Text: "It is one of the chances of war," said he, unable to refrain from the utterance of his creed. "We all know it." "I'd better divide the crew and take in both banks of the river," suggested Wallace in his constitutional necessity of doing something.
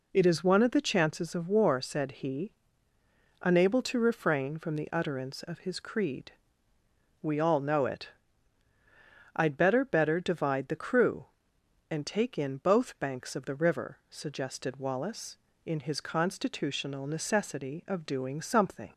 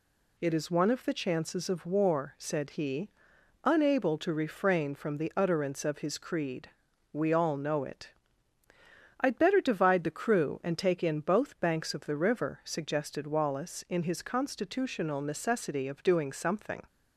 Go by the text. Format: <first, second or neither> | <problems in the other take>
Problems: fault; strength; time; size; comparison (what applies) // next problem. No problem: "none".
second | says "better" twice; at 9.8 s